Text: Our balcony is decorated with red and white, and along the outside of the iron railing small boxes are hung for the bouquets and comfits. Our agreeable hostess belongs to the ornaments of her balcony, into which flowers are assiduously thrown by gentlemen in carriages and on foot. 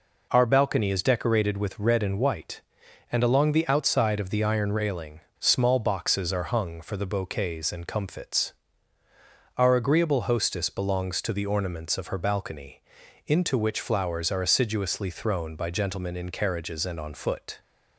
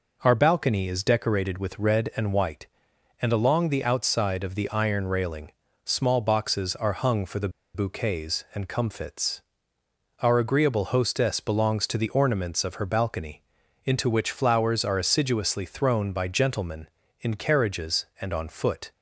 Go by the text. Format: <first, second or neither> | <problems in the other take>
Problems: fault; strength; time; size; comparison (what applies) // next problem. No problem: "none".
first | pauses between "railing" and "small"; slight; at 5.5 s; 0.34 s long; slight in the first // pauses between "the" and "bouquets"; slight; at 7.4 s; 0.26 s long